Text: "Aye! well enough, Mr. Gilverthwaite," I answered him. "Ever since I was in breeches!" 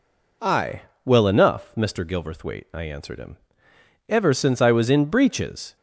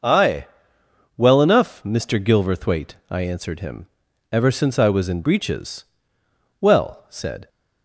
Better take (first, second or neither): first